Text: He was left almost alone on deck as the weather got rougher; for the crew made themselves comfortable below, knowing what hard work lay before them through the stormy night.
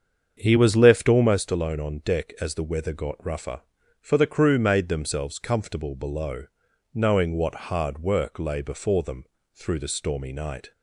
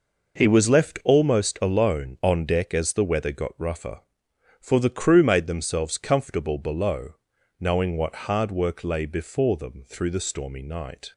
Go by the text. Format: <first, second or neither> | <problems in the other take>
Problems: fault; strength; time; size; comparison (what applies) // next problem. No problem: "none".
second | starts louder than the rest; strong; until 1.4 s; 7.5 dB // pauses between "them" and "through"; slight; at 9.2 s; 0.30 s long